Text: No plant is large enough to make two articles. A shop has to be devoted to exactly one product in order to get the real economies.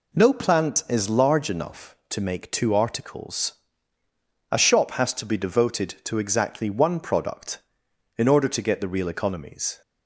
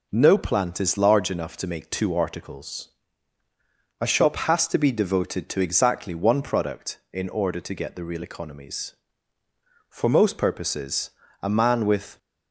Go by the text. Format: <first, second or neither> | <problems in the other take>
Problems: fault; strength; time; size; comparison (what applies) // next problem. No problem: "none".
first | goes on to say "For most purposes a man with"; strong; from 9.8 s on; 2.3 s long